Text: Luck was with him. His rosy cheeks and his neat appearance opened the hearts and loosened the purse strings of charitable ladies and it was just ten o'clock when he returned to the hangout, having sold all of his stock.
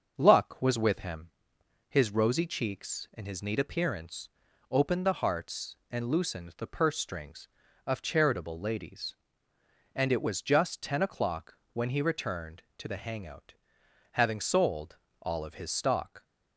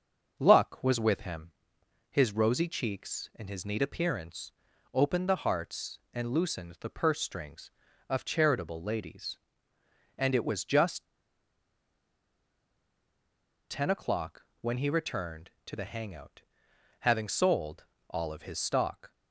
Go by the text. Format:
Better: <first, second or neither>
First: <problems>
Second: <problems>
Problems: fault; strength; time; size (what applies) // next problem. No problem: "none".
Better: first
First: starts louder than the rest; noticeable; until 1.1 s; 6 dB // pauses between "appearance" and "opened"; at 4.2 s; 0.42 s long // pauses between "o'clock" and "when"; slight; at 11.5 s; 0.16 s long // pauses between "sold" and "all"; slight; at 14.9 s; 0.24 s long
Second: starts louder than the rest; noticeable; until 1.4 s; 6 dB // pauses between "appearance" and "opened"; at 4.5 s; 0.42 s long // pauses between "just" and "ten"; strong; at 11.0 s; 2.6 s long // pauses between "o'clock" and "when"; slight; at 14.4 s; 0.16 s long // pauses between "sold" and "all"; slight; at 17.8 s; 0.24 s long